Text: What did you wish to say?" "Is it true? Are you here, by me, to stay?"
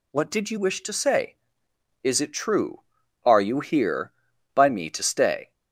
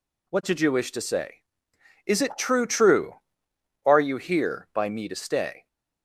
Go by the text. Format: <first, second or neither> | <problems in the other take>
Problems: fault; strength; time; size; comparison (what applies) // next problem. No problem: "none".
first | says "true" twice; at 2.6 s